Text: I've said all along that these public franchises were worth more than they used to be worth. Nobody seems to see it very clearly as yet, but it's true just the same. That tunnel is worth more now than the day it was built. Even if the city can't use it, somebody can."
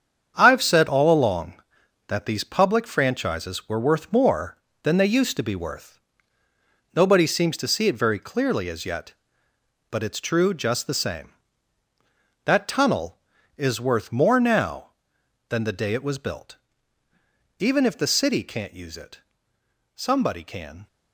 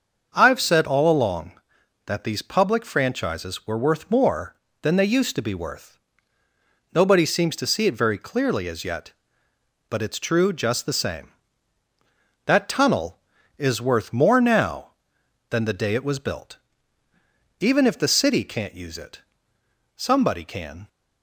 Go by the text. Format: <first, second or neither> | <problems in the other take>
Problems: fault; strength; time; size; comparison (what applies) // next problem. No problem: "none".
second | gets quieter; strong; throughout; 9 dB // starts louder than the rest; strong; until 1.3 s; 7.5 dB; also in the second